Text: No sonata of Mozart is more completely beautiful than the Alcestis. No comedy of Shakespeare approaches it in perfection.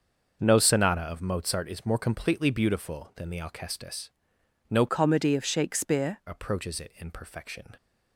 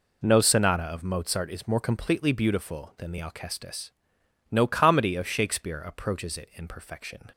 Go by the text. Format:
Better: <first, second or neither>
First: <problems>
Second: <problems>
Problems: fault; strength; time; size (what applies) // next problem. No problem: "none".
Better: second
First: starts louder than the rest; until 1.4 s; 6.5 dB // changes voice from "comedy" to "Shakespeare"; from 4.8 to 6.1 s; 1.3 s long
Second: none